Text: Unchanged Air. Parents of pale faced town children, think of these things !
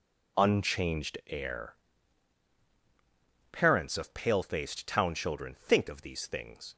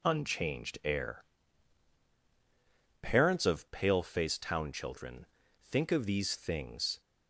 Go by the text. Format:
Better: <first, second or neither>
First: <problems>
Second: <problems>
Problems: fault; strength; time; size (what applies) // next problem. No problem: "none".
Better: neither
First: none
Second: none